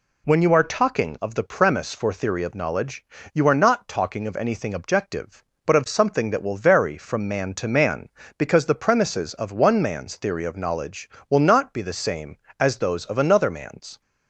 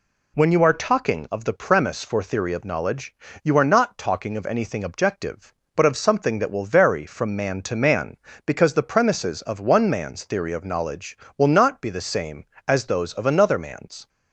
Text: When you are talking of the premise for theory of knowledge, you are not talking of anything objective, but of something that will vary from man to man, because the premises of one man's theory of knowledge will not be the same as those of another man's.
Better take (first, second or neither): neither